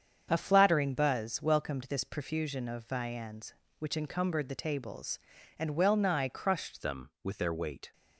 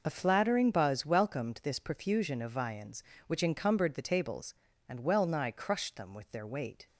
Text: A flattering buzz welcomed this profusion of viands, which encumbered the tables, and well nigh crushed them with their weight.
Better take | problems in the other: second | starts louder than the rest; strong; until 1.3 s; 7.5 dB // changes voice at "them"; from 6.8 s on; 1.1 s long

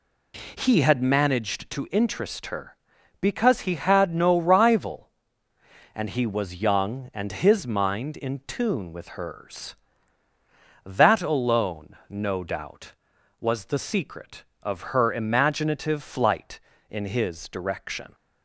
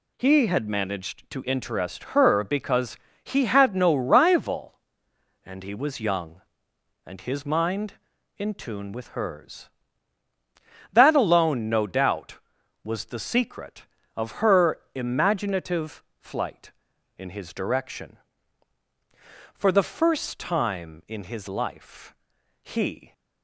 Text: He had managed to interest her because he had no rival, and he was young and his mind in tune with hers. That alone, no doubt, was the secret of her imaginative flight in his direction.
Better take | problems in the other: first | pauses between "because" and "he"; slight; at 2.9 s; 0.28 s long // pauses between "imaginative" and "flight"; slight; at 16.0 s; 0.16 s long // goes on to say "For the first time in his life he"; strong; from 19.5 s on; 3.6 s long

